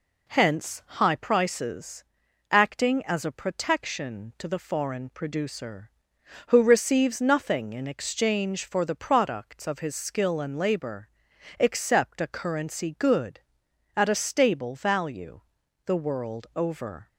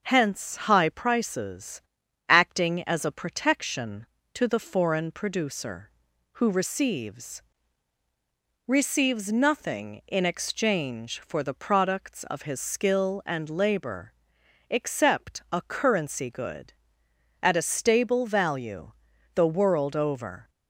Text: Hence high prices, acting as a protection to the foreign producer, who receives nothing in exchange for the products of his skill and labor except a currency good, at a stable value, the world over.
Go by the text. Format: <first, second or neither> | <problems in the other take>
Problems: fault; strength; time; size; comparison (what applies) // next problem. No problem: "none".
first | starts louder than the rest; until 1.0 s; 6.5 dB // says "receives" twice; at 8.6 s // pauses between "labor" and "except"; noticeable; at 14.1 s; 0.56 s long; noticeable in the first